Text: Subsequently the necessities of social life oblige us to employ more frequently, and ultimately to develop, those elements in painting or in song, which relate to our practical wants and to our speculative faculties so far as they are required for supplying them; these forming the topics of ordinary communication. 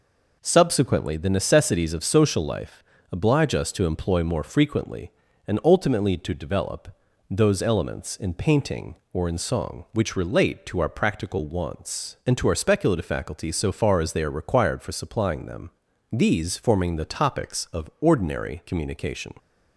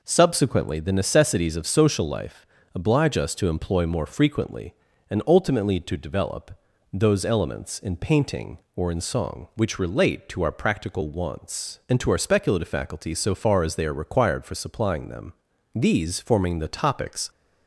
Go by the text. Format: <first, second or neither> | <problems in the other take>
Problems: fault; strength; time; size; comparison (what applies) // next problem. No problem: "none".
first | pauses between "life" and "oblige"; slight; at 2.4 s; 0.28 s long; slight in the first // stops before "of ordinary communication"; at 17.2 s